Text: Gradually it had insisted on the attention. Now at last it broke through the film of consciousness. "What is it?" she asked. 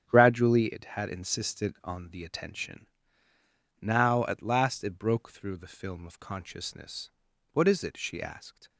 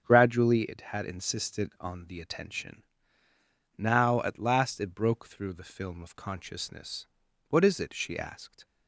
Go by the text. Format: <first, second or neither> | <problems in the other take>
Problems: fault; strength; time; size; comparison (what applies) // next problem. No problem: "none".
second | gets quieter; strong; throughout; 9.5 dB // starts louder than the rest; strong; until 1.0 s; 8.5 dB; strong in the second